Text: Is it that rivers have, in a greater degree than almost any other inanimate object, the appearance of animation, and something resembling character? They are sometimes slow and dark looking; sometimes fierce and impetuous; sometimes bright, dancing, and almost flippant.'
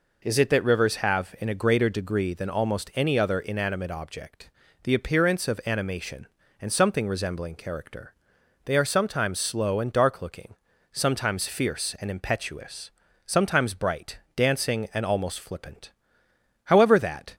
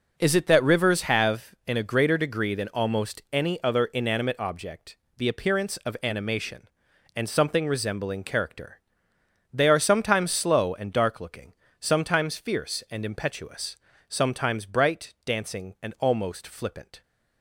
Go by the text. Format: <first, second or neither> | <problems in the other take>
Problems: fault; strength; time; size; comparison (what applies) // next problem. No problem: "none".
second | goes on to say "However that"; noticeable; from 16.6 s on; 0.70 s long